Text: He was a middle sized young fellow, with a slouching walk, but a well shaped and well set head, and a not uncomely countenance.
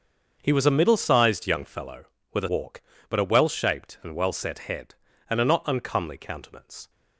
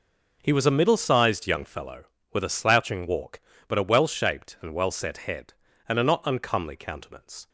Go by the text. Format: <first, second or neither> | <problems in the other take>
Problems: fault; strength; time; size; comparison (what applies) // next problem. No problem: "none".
second | starts louder than the rest; until 1.4 s; 6.5 dB // skips "slouching"; at 2.4 s